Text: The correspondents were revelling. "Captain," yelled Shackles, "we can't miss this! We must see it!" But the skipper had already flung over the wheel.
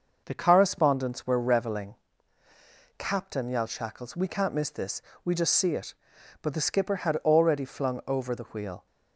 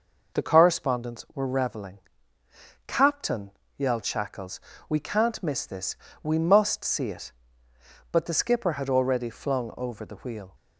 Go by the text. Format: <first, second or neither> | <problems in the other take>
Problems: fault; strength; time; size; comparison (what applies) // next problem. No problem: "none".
second | says "just" for "must"; at 5.3 s